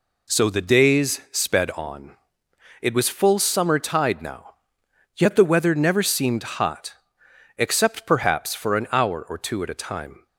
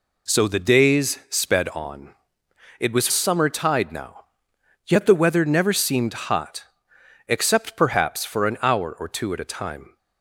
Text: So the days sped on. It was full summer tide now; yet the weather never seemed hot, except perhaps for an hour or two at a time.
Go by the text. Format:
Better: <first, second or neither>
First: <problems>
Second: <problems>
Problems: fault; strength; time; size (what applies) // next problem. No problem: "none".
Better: first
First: none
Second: skips "full"; at 3.0 s